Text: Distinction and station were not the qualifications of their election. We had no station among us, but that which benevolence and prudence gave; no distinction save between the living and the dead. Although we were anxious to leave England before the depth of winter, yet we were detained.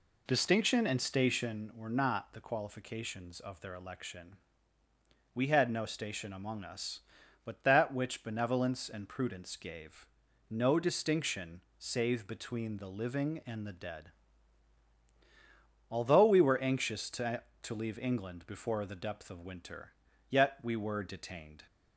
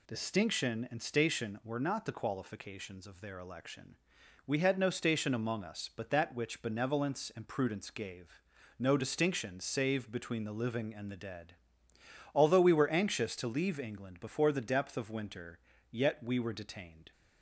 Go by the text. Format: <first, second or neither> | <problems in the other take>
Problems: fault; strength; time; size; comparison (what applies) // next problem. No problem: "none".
second | pauses between "distinction" and "save"; slight; at 11.5 s; 0.18 s long // says "to" twice; at 17.6 s